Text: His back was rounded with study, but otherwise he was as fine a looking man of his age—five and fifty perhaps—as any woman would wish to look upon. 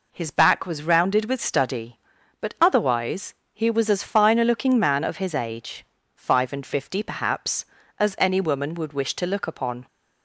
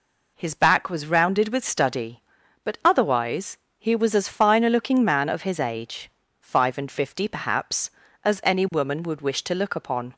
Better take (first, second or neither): neither